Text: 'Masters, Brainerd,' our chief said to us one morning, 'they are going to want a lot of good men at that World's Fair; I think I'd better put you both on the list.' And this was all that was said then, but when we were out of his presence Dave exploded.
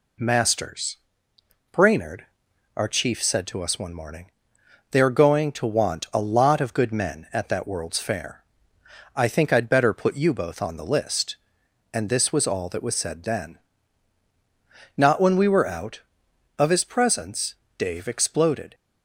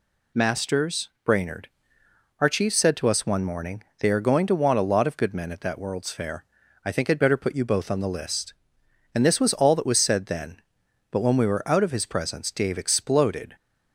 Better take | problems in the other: second | says "not" for "but"; at 14.9 s // pauses between "presence" and "Dave"; slight; at 17.5 s; 0.24 s long

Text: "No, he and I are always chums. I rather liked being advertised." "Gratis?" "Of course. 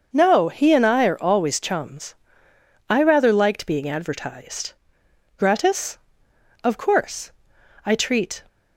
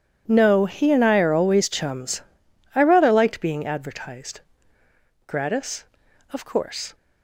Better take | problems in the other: second | starts louder than the rest; noticeable; until 1.1 s; 6 dB // goes on to say "I treat"; from 7.8 s on; 0.58 s long

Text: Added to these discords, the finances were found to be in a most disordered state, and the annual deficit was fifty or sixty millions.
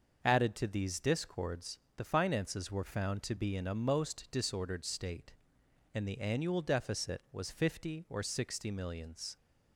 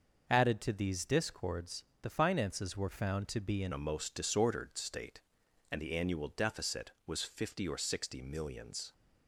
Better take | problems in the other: first | starts louder than the rest; noticeable; until 1.2 s; 6 dB; also in the first // changes voice at "a"; from 3.7 s on; 5.2 s long

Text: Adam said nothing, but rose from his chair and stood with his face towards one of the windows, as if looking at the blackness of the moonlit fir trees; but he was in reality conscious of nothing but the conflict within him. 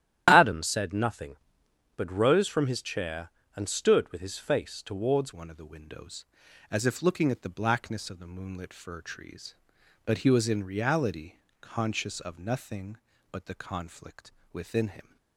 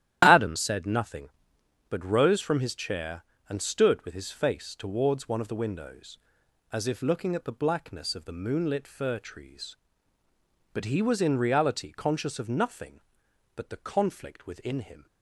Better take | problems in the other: second | starts louder than the rest; strong; until 1.2 s; 11.5 dB; strong in the second // changes voice at "one"; from 5.3 s on; 9.8 s long // pauses between "reality" and "conscious"; slight; at 11.3 s; 0.26 s long // pauses between "conflict" and "within"; slight; at 14.3 s; 0.22 s long

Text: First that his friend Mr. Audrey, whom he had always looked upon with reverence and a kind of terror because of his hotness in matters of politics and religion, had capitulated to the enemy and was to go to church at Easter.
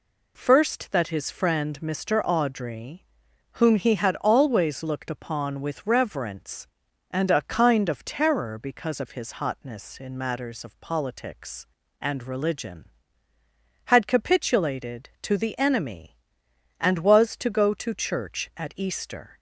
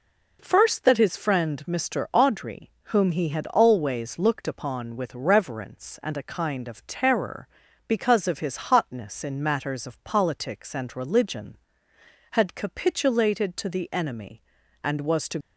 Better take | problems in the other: first | stops before "go to church at Easter"; at 15.4 s

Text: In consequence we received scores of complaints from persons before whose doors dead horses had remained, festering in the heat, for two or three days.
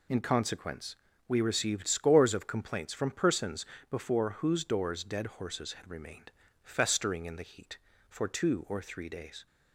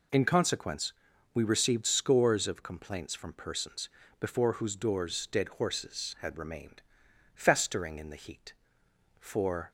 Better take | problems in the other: first | pauses between "consequence" and "we"; at 0.9 s; 0.44 s long; slight in the first // pauses between "persons" and "before"; slight; at 3.8 s; 0.32 s long; slight in the first // stops before "two or three days"; at 9.6 s

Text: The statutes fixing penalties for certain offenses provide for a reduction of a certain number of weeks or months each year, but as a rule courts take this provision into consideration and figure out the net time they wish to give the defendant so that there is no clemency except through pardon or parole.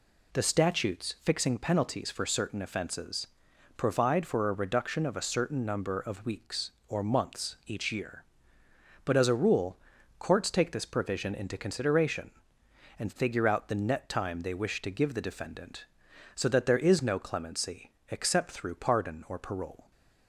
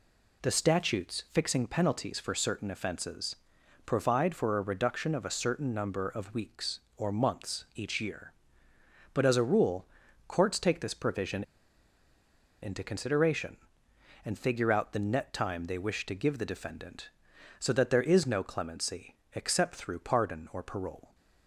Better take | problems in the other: first | pauses between "offenses" and "provide"; noticeable; at 3.3 s; 0.50 s long; noticeable in the first // pauses between "rule" and "courts"; at 9.8 s; 0.44 s long; also in the first // pauses between "provision" and "into"; at 11.4 s; 1.1 s long // pauses between "clemency" and "except"; slight; at 19.1 s; 0.18 s long; slight in the first

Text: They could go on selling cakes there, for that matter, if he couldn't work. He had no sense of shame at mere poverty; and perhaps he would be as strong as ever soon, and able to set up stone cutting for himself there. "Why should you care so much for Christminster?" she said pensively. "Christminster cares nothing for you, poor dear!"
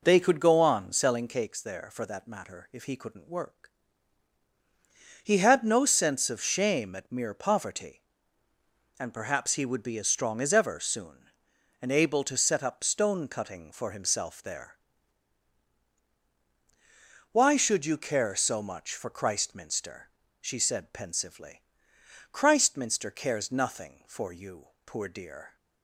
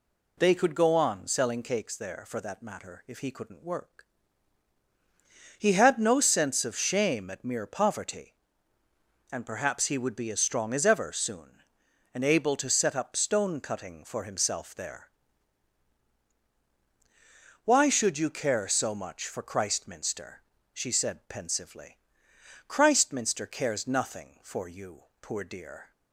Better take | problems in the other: second | starts louder than the rest; noticeable; until 1.3 s; 4 dB

